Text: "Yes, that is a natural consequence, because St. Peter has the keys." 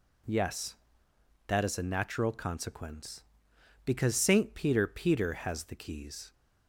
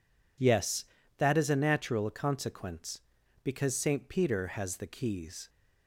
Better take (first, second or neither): second